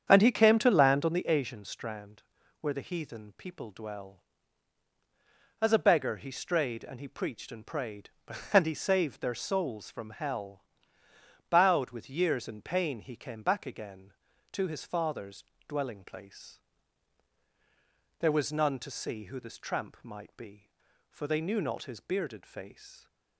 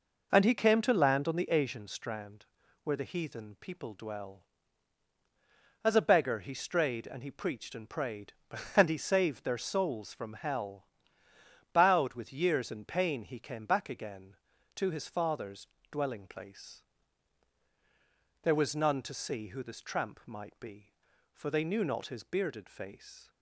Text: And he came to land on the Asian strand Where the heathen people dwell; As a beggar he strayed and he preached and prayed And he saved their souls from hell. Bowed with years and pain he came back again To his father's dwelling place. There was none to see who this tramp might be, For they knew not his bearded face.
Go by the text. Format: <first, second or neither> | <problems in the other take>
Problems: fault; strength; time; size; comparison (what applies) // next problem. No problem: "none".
second | starts louder than the rest; strong; until 1.2 s; 8 dB // pauses between "strand" and "Where"; at 2.2 s; 0.38 s long; also in the second // pauses between "father's" and "dwelling"; slight; at 15.4 s; 0.24 s long; slight in the second